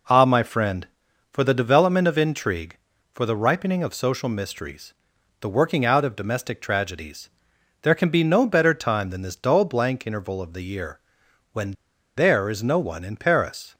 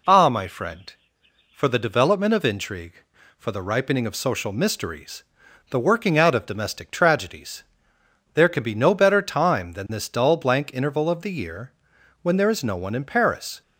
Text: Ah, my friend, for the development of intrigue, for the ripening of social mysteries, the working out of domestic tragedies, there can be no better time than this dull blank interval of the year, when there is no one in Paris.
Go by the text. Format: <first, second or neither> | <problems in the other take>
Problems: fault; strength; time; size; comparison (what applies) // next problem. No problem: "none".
second | pauses between "when" and "there"; at 11.7 s; 0.42 s long